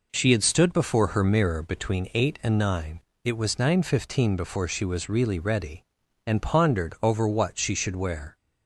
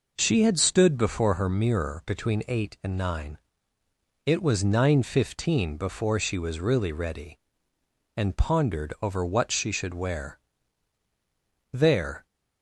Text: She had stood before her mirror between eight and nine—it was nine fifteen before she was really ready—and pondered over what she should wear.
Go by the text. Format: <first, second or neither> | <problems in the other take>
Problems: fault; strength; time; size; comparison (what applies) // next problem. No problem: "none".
first | goes on to say "There"; from 11.7 s on; 0.52 s long